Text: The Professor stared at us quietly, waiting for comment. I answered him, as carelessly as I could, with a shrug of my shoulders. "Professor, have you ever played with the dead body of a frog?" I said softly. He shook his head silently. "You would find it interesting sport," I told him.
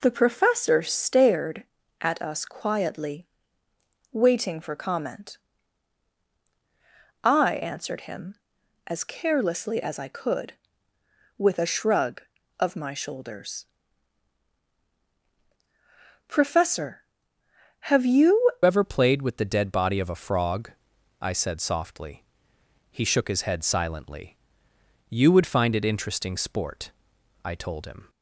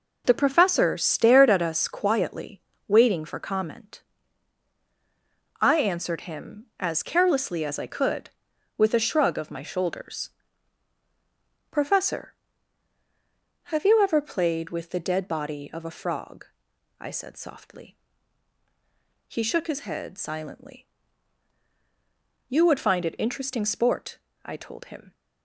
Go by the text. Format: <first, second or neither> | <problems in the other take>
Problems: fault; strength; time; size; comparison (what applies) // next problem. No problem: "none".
second | changes voice at "ever"; from 18.6 s on; 9.4 s long